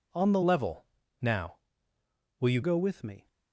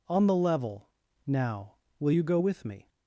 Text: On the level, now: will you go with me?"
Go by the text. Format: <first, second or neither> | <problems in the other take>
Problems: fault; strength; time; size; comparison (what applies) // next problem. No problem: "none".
second | changes voice from "level" to "you"; from 0.4 to 2.6 s; 2.2 s long